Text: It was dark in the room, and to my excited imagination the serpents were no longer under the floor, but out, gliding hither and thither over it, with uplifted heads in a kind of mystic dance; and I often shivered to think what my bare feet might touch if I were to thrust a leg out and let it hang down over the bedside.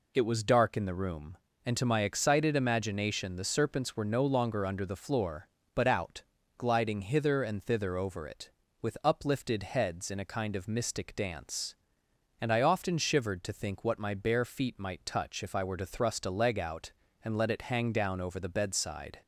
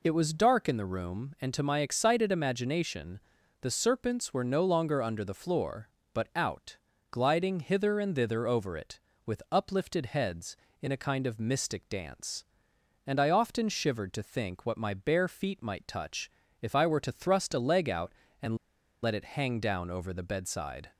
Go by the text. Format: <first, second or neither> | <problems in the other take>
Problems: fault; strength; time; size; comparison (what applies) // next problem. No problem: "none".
first | pauses between "imagination" and "the"; at 3.1 s; 0.40 s long // pauses between "touch" and "if"; slight; at 16.3 s; 0.30 s long // pauses between "and" and "let"; noticeable; at 18.5 s; 0.46 s long